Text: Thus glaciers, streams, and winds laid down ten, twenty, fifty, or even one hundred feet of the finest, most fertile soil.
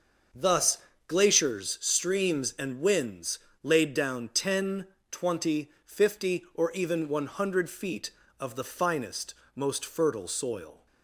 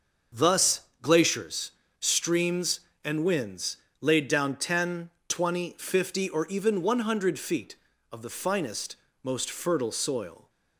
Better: neither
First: starts louder than the rest; until 1.6 s; 6.5 dB // pauses between "Thus" and "glaciers"; slight; at 0.7 s; 0.30 s long // pauses between "winds" and "laid"; slight; at 3.3 s; 0.24 s long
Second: starts louder than the rest; until 1.5 s; 6.5 dB // pauses between "Thus" and "glaciers"; slight; at 0.8 s; 0.22 s long // pauses between "winds" and "laid"; slight; at 3.7 s; 0.24 s long

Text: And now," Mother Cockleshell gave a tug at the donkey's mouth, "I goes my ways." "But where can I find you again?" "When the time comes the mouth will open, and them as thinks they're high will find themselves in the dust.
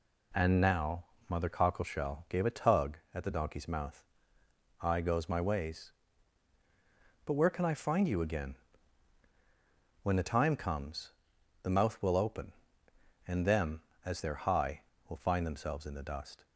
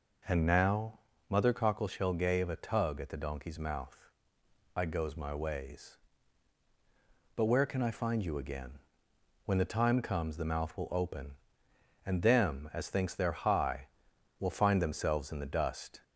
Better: second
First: pauses between "comes" and "the"; noticeable; at 11.1 s; 0.48 s long // skips "thinks"; at 14.2 s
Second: none

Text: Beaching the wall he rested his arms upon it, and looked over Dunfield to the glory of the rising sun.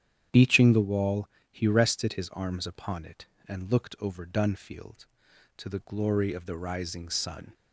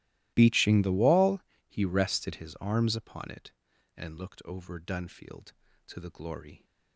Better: first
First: starts louder than the rest; strong; until 1.5 s; 10 dB // pauses between "wall" and "he"; slight; at 1.2 s; 0.22 s long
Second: starts louder than the rest; strong; until 1.3 s; 17 dB // pauses between "wall" and "he"; slight; at 1.4 s; 0.28 s long // stops before "of the rising sun"; at 6.6 s

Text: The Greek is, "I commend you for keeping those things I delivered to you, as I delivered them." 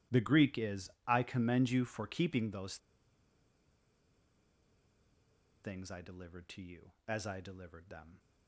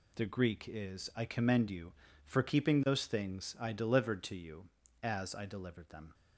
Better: second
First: pauses between "those" and "things"; strong; at 2.7 s; 2.8 s long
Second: none

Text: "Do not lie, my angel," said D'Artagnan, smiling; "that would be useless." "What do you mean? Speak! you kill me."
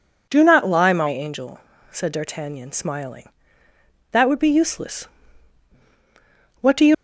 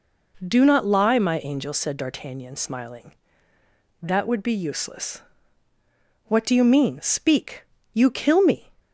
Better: second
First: stops before "mean Speak you kill me"; at 6.9 s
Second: none

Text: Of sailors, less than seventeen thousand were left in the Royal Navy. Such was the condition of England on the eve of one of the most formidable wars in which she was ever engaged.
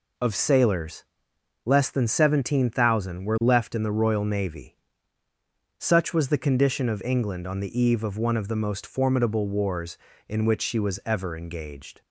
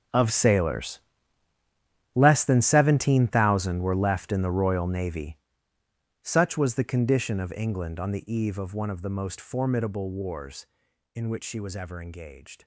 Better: first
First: none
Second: gets quieter; strong; throughout; 16 dB

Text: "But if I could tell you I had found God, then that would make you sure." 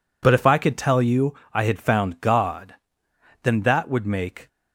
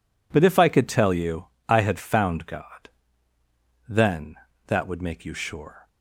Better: second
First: pauses between "you" and "I"; slight; at 1.3 s; 0.18 s long // stops before "you sure"; at 4.4 s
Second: pauses between "you" and "I"; slight; at 1.4 s; 0.20 s long

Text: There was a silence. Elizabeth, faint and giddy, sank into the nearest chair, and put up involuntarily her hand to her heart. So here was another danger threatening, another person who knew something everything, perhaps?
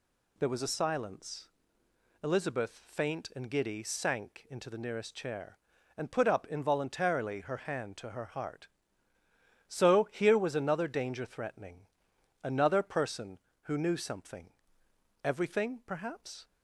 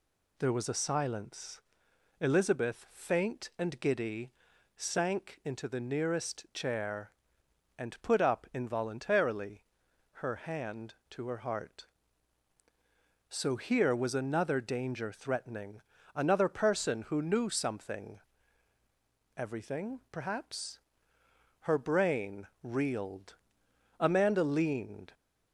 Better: first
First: pauses between "something" and "everything"; noticeable; at 14.4 s; 0.74 s long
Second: pauses between "involuntarily" and "her"; noticeable; at 9.6 s; 0.58 s long // pauses between "something" and "everything"; at 18.1 s; 1.2 s long // goes on to say "Her brain reeled Amanda leaned"; strong; from 21.6 s on; 3.5 s long

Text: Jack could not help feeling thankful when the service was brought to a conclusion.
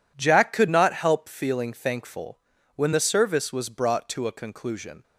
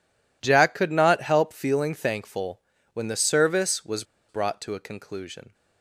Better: first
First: pauses between "thankful" and "when"; at 2.3 s; 0.38 s long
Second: pauses between "thankful" and "when"; slight; at 2.6 s; 0.34 s long // pauses between "was" and "brought"; slight; at 4.0 s; 0.25 s long

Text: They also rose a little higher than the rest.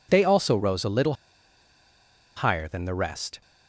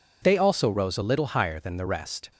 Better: second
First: pauses between "little" and "higher"; at 1.1 s; 1.2 s long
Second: none

